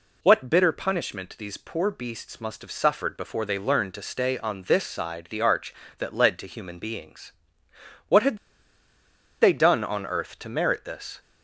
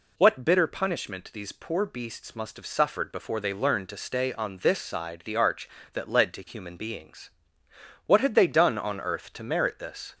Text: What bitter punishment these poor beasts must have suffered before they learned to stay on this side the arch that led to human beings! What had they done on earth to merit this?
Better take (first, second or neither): second